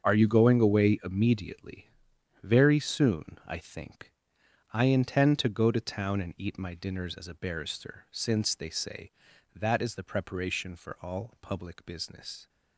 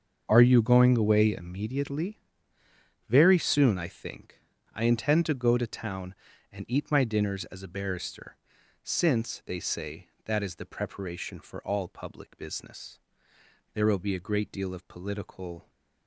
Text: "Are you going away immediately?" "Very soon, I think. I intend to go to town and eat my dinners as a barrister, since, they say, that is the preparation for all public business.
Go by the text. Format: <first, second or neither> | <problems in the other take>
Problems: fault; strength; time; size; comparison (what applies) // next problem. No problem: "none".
first | starts louder than the rest; until 1.2 s; 6.5 dB; also in the first // goes on to say "There will be a great deal of political"; strong; from 13.7 s on; 1.9 s long